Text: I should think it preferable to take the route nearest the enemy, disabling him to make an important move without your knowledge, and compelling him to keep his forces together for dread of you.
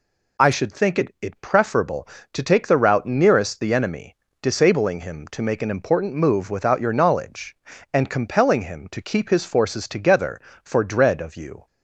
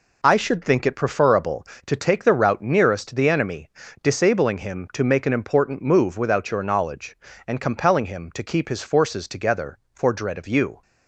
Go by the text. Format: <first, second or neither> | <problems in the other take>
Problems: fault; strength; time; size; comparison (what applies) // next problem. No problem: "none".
second | says "it" twice; at 1.2 s